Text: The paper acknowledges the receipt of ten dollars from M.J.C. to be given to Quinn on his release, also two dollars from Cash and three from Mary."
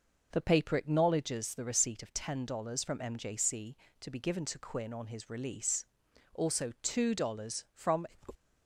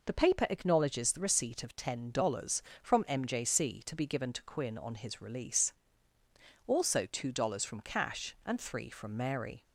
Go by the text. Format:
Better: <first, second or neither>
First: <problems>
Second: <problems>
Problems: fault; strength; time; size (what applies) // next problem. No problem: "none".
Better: second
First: stops before "Cash and three from Mary"; at 8.3 s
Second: none